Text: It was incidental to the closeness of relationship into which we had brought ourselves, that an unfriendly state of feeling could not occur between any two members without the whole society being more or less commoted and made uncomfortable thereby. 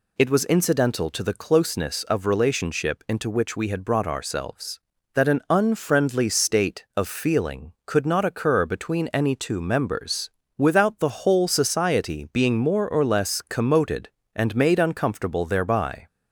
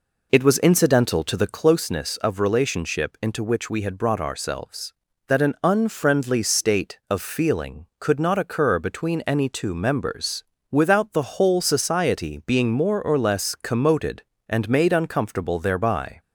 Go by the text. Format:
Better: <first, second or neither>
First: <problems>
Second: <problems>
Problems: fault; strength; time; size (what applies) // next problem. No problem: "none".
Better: first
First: pauses between "members" and "without"; slight; at 10.3 s; 0.26 s long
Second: starts louder than the rest; noticeable; until 1.8 s; 4 dB // pauses between "members" and "without"; slight; at 10.4 s; 0.26 s long